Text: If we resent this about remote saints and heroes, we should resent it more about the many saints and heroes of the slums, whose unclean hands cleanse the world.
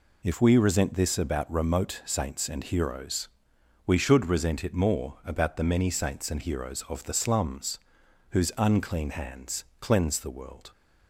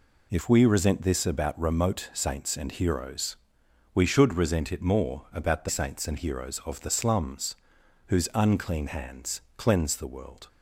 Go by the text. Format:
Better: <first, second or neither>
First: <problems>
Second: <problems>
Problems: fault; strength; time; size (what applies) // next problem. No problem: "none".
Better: first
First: pauses between "hands" and "cleanse"; slight; at 9.6 s; 0.16 s long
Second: skips "many"; at 5.6 s // pauses between "hands" and "cleanse"; slight; at 9.3 s; 0.16 s long